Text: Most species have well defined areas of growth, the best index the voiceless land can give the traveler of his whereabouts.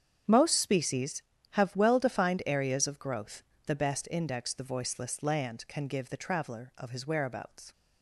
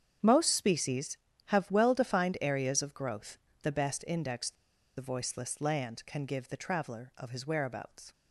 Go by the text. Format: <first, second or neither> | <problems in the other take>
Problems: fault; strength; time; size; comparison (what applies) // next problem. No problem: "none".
first | starts louder than the rest; strong; until 1.5 s; 8 dB; strong in the first // pauses between "the" and "voiceless"; at 4.5 s; 0.44 s long